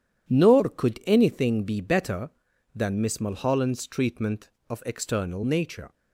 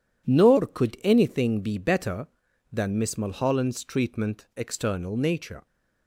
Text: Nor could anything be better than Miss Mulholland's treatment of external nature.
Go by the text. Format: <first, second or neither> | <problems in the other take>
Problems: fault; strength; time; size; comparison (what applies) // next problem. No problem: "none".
first | skips "of"; at 4.5 s